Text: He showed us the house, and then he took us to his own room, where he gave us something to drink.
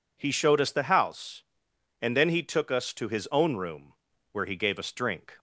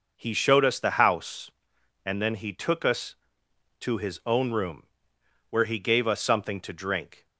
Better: second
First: skips "something to"; at 4.9 s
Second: none

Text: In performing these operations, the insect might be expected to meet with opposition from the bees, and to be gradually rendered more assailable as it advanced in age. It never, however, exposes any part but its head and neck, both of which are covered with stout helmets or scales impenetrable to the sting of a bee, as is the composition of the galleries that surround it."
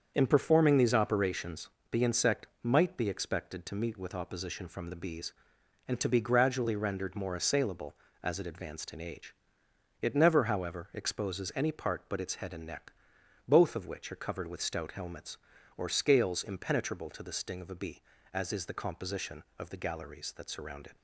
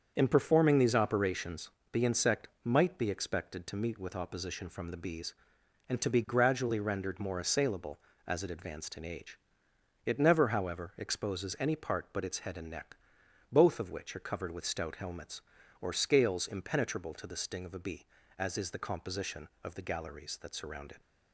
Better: neither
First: starts louder than the rest; strong; until 1.1 s; 7 dB // pauses between "insect" and "might"; slight; at 2.4 s; 0.16 s long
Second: starts louder than the rest; strong; until 1.1 s; 7 dB // pauses between "insect" and "might"; slight; at 2.4 s; 0.16 s long

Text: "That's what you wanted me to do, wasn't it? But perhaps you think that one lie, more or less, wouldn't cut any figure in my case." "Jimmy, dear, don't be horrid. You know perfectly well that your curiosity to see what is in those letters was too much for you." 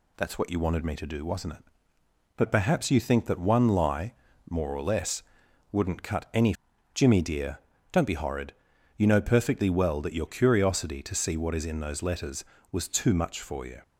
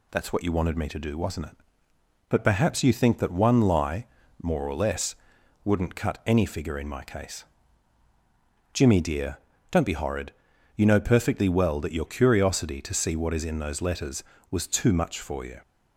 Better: second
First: skips "figure in my case"; at 6.7 s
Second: none

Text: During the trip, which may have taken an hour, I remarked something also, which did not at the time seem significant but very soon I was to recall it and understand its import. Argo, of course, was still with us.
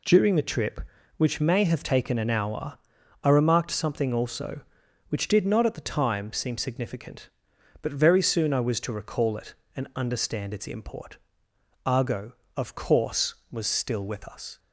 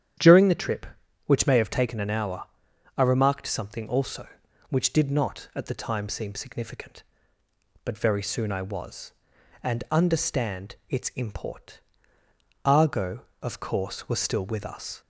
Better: first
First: none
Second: starts louder than the rest; strong; until 1.6 s; 9.5 dB // skips "to recall it"; at 9.3 s // pauses between "understand" and "its"; slight; at 10.7 s; 0.16 s long

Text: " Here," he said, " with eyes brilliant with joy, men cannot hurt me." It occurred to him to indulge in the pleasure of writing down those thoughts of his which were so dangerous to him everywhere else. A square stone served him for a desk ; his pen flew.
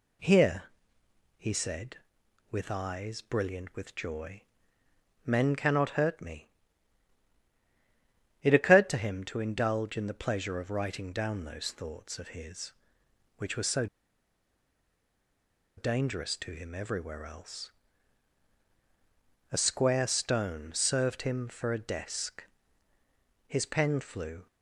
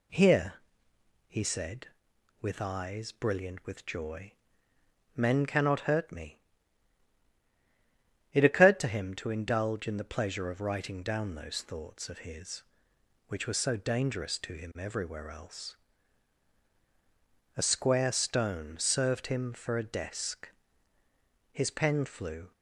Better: second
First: pauses between "so" and "dangerous"; strong; at 13.8 s; 1.9 s long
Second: none

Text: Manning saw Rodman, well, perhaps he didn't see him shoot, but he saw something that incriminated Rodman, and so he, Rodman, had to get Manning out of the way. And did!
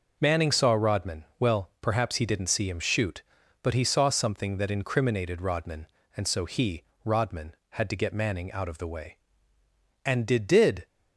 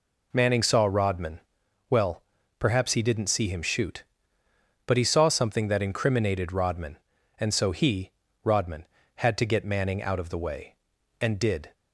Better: second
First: says "did" twice; at 10.4 s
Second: none

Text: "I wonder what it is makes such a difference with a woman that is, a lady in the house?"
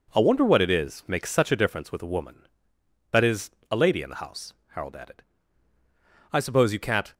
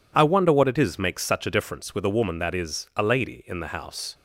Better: second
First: goes on to say "Harold added I suppose you can't"; strong; from 4.6 s on; 2.4 s long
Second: none

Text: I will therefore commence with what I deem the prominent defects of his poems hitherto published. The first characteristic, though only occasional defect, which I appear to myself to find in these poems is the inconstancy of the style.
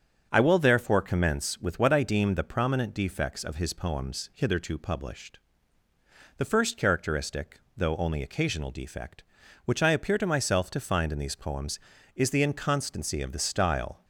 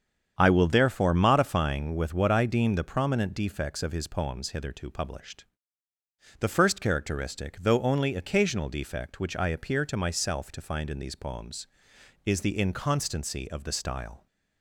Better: first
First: starts louder than the rest; until 1.3 s; 7 dB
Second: starts louder than the rest; strong; until 1.3 s; 7.5 dB // says "modifying" for "commence"; at 1.1 s

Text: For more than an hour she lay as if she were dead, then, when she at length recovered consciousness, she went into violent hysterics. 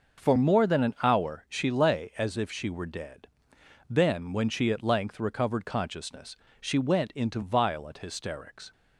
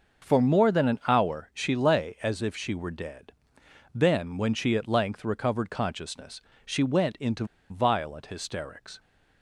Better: first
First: none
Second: pauses between "into" and "violent"; slight; at 7.4 s; 0.25 s long

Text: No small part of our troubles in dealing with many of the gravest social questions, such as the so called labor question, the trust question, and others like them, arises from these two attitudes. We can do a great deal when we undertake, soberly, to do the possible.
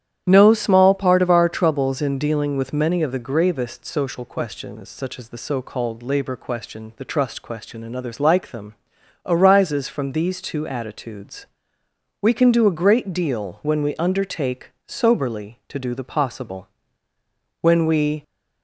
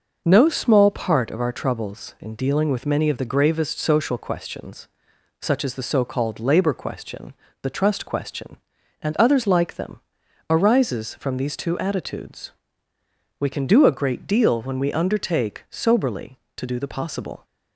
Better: second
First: starts louder than the rest; strong; until 1.2 s; 10.5 dB // goes on to say "When we"; noticeable; from 17.6 s on; 0.62 s long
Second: none

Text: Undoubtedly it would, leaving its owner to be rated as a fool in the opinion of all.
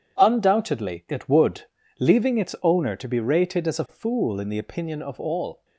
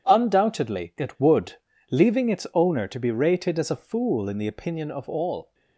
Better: neither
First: none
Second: none

